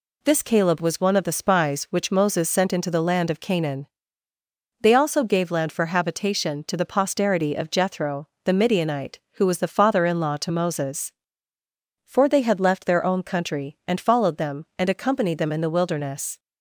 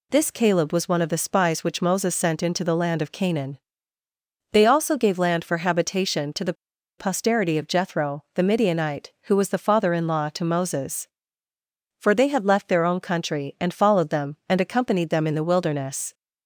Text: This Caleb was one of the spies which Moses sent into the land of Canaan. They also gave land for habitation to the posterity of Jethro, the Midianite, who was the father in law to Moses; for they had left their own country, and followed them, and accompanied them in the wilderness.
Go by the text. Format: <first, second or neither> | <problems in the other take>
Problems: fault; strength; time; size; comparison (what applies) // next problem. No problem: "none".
first | pauses between "the" and "posterity"; at 6.5 s; 0.44 s long